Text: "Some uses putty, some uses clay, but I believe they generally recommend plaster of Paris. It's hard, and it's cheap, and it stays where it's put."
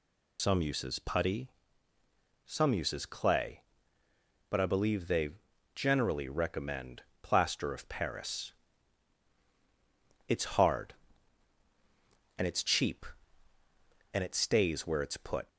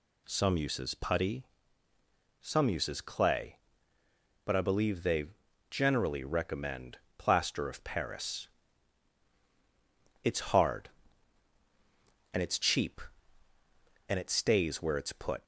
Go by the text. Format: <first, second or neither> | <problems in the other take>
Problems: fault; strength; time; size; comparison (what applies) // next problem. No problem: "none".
second | loses the start of "Some"; at 0.3 s; 90 ms // pauses between "they" and "generally"; at 5.3 s; 0.42 s long; also in the second // pauses between "recommend" and "plaster"; slight; at 7.0 s; 0.22 s long; slight in the second